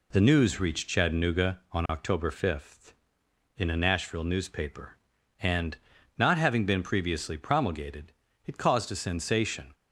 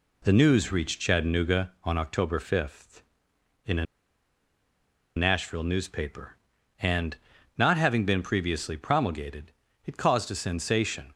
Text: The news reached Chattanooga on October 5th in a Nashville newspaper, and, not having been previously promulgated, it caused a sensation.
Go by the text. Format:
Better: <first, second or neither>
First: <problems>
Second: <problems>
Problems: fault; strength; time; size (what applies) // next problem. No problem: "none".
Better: first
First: none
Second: pauses between "a" and "Nashville"; strong; at 3.8 s; 1.3 s long